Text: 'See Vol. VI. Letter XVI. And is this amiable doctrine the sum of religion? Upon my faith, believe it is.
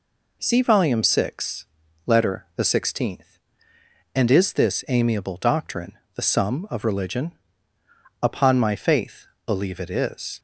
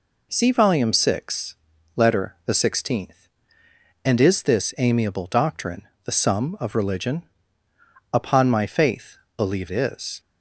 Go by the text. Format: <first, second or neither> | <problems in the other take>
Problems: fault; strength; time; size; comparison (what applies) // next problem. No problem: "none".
first | pauses between "doctrine" and "the"; slight; at 5.8 s; 0.16 s long; slight in the first // skips "it"; at 9.6 s